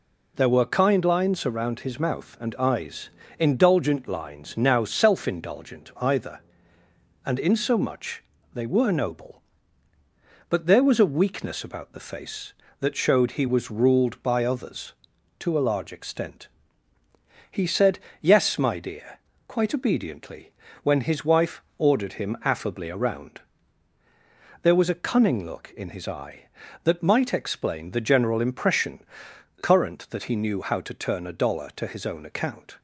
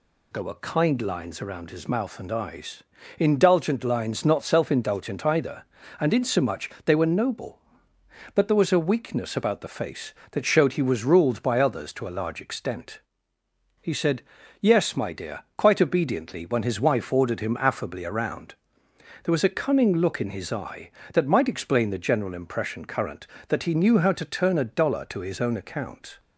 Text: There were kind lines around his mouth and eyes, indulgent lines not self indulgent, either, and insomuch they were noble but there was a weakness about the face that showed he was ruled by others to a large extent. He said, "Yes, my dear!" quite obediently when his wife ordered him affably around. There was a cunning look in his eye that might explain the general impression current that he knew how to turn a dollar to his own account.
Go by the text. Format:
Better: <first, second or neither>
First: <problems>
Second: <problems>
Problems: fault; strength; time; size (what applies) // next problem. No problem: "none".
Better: second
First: says "now" for "not"; at 4.5 s // pauses between "insomuch" and "they"; slight; at 8.2 s; 0.30 s long // pauses between "obediently" and "when"; slight; at 20.5 s; 0.30 s long // pauses between "wife" and "ordered"; slight; at 21.6 s; 0.16 s long // pauses between "impression" and "current"; noticeable; at 29.0 s; 0.60 s long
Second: none